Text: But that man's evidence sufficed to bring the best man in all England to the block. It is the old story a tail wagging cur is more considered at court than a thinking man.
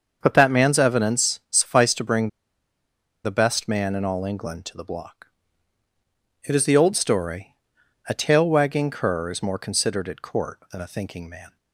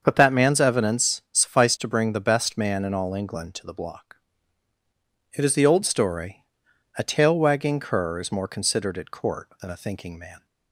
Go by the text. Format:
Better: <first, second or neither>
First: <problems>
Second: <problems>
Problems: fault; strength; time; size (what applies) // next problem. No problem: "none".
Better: second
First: starts louder than the rest; until 1.2 s; 6.5 dB // pauses between "bring" and "the"; noticeable; at 2.2 s; 0.96 s long // pauses between "story" and "a"; noticeable; at 7.5 s; 0.54 s long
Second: starts louder than the rest; until 1.0 s; 6.5 dB // pauses between "story" and "a"; noticeable; at 6.4 s; 0.54 s long